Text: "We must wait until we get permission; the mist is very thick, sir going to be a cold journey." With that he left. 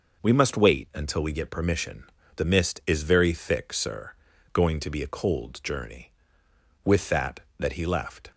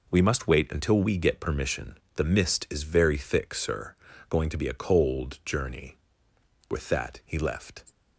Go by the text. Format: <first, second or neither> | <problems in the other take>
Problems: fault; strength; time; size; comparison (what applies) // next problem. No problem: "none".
second | pauses between "sir" and "going"; slight; at 4.1 s; 0.36 s long; slight in the second // says "that" twice; at 7.5 s